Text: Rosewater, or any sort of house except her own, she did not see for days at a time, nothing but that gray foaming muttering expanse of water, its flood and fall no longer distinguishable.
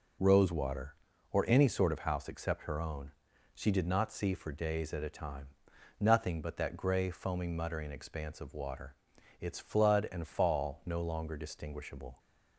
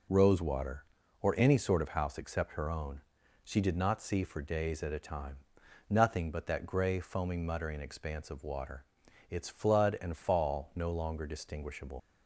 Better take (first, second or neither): first